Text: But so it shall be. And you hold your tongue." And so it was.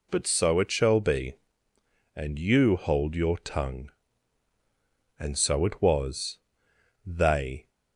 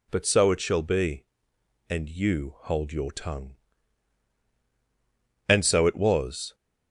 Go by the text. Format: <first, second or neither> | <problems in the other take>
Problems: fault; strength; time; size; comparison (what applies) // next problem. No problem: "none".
second | goes on to say "They"; noticeable; from 7.0 s on; 0.64 s long